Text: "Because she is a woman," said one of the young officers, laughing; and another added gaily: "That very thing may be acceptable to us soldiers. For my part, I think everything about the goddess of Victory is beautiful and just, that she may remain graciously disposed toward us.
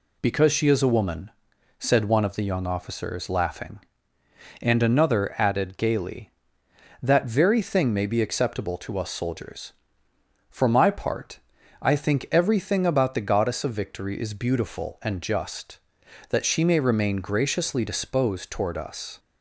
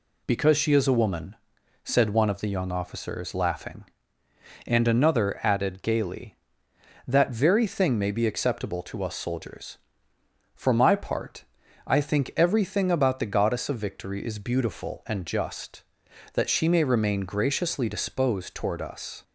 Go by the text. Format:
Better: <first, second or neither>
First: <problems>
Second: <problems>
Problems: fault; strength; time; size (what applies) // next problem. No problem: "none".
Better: neither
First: none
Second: none